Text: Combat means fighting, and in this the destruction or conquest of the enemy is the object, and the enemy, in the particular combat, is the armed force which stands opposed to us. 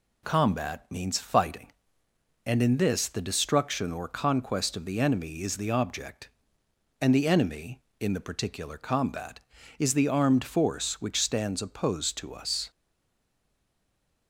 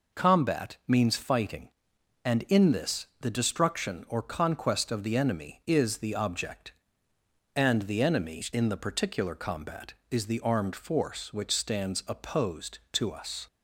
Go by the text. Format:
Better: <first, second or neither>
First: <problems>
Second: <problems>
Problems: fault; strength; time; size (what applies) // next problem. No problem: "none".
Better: second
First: stays silent after the last word; noticeable; from 12.7 s on; 1.5 s long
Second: none